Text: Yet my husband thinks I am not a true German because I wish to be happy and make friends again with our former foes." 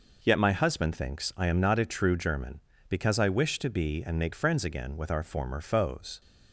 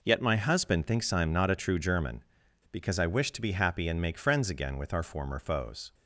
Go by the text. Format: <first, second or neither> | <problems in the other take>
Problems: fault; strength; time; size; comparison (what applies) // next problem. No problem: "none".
second | skips "happy"; at 4.0 s